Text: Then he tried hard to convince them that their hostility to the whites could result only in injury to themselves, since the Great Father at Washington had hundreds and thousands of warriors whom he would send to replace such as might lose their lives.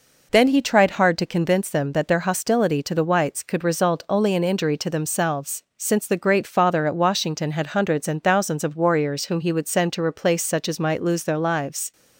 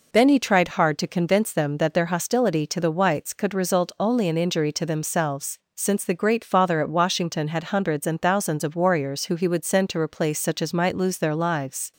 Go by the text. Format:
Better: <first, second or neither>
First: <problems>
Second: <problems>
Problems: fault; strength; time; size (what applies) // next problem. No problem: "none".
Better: first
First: none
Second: says "who" for "whom"; at 9.2 s